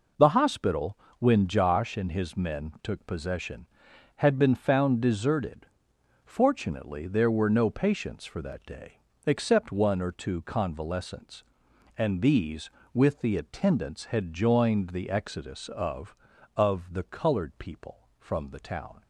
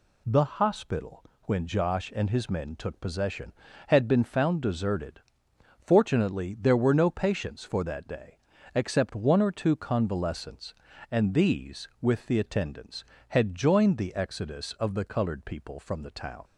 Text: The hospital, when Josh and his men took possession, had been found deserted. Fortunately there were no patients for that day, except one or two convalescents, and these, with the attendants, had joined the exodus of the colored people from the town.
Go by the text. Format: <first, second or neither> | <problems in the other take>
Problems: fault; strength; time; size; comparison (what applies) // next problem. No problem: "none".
second | says "of" twice; at 16.5 s